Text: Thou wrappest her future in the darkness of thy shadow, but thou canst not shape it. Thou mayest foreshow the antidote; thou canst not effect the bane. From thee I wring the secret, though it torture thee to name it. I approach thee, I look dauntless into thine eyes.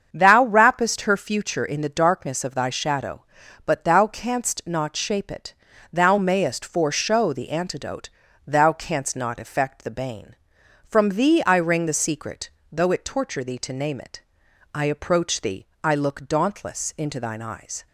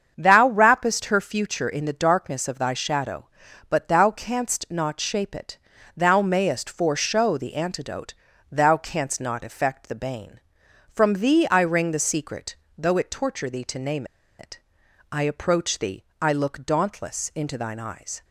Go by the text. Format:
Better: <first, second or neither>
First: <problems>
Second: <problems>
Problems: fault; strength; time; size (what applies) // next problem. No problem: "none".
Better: first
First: starts louder than the rest; strong; until 1.1 s; 7.5 dB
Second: starts louder than the rest; strong; until 1.1 s; 7.5 dB // pauses between "name" and "it"; slight; at 14.0 s; 0.34 s long